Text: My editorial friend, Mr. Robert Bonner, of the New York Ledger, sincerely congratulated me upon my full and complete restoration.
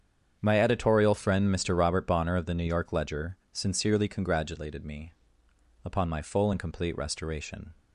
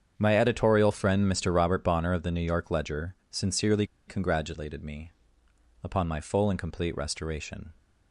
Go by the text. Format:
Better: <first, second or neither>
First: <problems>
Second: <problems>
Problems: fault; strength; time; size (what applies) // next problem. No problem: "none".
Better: first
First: starts louder than the rest; strong; until 1.4 s; 7.5 dB // pauses between "me" and "upon"; noticeable; at 5.1 s; 0.70 s long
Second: starts louder than the rest; strong; until 1.1 s; 7.5 dB // pauses between "sincerely" and "congratulated"; slight; at 3.8 s; 0.22 s long // pauses between "me" and "upon"; noticeable; at 5.1 s; 0.70 s long